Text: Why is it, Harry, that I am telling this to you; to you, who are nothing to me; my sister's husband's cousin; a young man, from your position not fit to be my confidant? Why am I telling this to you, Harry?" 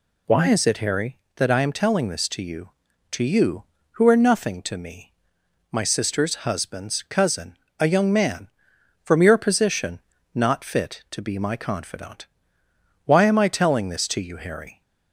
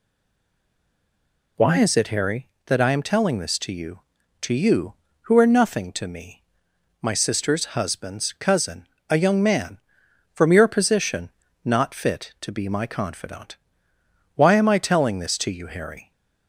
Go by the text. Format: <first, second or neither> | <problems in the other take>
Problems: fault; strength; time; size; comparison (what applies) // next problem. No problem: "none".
first | stays silent before the first word; noticeable; until 1.5 s; 1.5 s long // pauses between "position" and "not"; slight; at 11.2 s; 0.34 s long; slight in the first